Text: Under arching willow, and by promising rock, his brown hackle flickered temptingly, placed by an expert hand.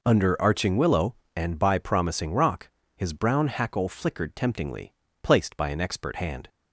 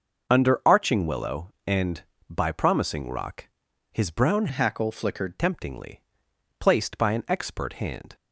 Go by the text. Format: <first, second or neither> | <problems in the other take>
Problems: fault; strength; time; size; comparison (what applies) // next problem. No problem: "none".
first | changes voice from "hackle" to "flickered"; from 4.4 to 5.3 s; 0.9 s long